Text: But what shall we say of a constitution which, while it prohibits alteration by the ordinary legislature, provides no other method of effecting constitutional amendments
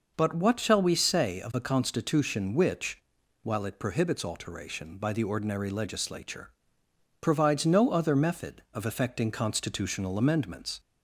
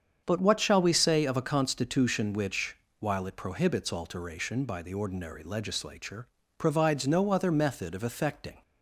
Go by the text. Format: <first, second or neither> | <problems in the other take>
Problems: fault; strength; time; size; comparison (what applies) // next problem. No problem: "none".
first | starts louder than the rest; strong; until 1.2 s; 7.5 dB // stops before "constitutional amendments"; at 8.6 s